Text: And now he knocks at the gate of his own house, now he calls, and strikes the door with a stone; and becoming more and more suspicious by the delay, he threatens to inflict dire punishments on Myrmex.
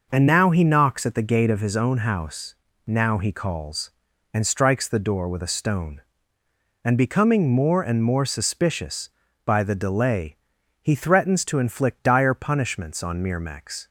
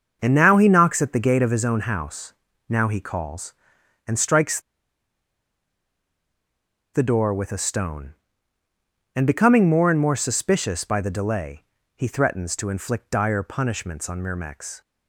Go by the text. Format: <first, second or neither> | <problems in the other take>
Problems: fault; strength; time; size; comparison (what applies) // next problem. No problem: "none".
first | starts louder than the rest; until 1.2 s; 6.5 dB // pauses between "strikes" and "the"; strong; at 4.5 s; 2.3 s long